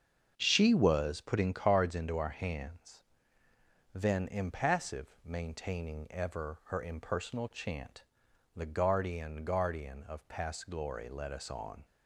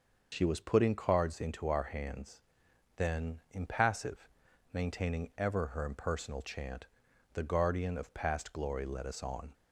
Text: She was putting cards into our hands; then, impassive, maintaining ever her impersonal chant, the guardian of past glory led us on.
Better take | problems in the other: second | starts louder than the rest; until 1.3 s; 7 dB; also in the second // says "guardian" twice; at 9.4 s

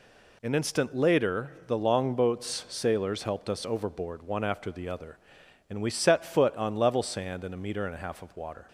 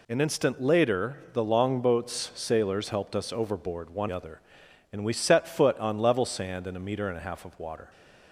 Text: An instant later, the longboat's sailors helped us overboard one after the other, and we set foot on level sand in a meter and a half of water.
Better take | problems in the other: first | skips "after the"; at 4.0 s

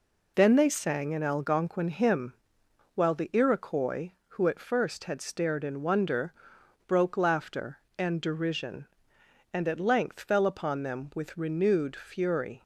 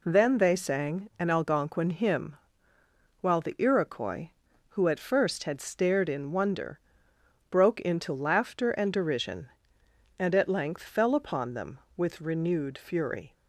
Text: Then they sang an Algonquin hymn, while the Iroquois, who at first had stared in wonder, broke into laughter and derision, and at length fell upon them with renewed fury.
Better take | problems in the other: second | skips "into"; at 7.1 s

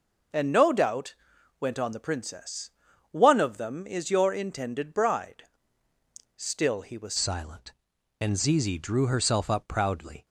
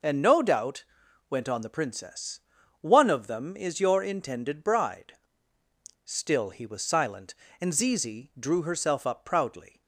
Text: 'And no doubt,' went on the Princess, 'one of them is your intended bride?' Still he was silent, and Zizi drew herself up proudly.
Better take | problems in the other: second | changes voice at "silent"; from 7.1 s on; 3.1 s long

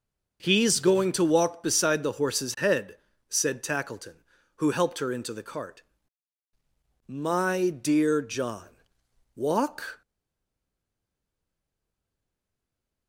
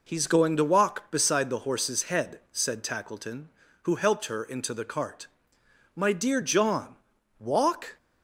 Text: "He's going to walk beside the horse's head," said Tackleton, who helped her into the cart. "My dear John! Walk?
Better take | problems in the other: second | stays silent after the last word; strong; from 10.0 s on; 3.0 s long

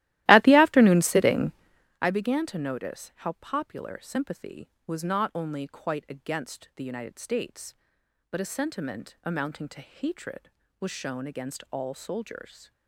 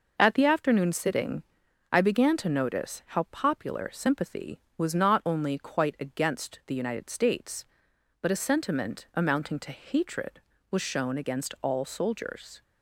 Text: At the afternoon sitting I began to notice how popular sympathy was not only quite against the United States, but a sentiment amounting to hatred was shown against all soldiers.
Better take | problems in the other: second | starts louder than the rest; strong; until 2.1 s; 16 dB // pauses between "sitting" and "I"; noticeable; at 1.5 s; 0.50 s long; noticeable in the second

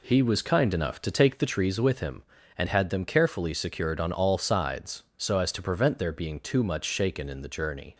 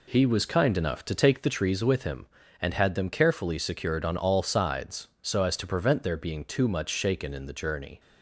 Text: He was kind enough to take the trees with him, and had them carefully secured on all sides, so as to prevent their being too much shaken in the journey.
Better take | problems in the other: neither | none

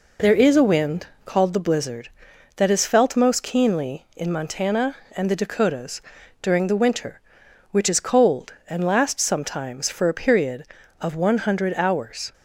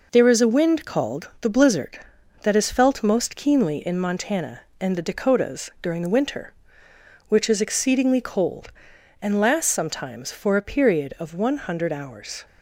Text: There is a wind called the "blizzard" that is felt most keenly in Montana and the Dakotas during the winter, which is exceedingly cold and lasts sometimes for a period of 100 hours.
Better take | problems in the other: second | pauses between "wind" and "called"; slight; at 1.0 s; 0.18 s long // pauses between "Dakotas" and "during"; at 6.0 s; 0.40 s long // skips "exceedingly"; at 8.0 s

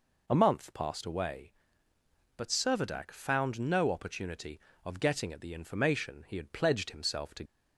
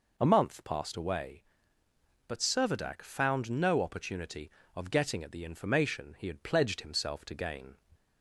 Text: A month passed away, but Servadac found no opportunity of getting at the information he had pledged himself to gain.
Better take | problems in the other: second | stops before "gain"; at 7.4 s

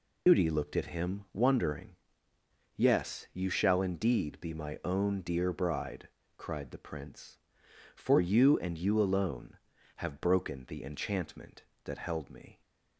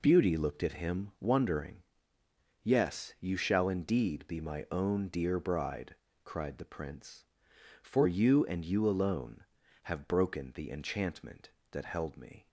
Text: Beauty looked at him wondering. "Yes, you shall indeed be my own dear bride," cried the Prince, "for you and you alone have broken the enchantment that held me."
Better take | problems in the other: second | loses the start of "Beauty"; at 0.2 s; 120 ms

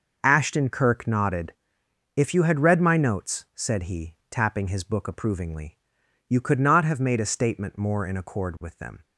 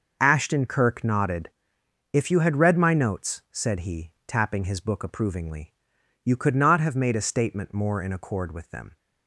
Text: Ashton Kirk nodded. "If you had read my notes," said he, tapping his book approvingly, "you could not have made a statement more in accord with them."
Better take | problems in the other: neither | none

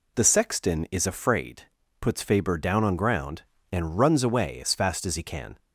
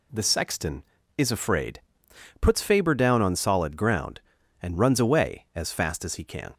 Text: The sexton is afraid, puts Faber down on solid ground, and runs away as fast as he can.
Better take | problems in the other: second | skips "solid"; at 2.9 s

